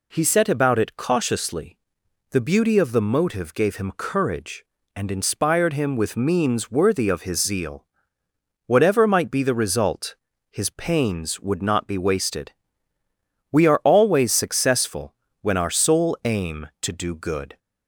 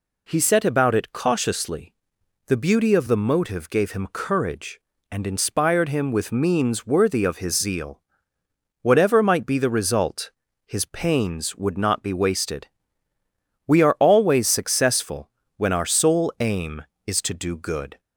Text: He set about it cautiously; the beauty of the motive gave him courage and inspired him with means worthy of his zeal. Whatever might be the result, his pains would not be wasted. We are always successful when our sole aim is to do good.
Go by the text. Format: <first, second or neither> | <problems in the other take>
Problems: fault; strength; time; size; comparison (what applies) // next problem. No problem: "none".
second | pauses between "successful" and "when"; slight; at 15.1 s; 0.28 s long; slight in the second // skips "is"; at 16.7 s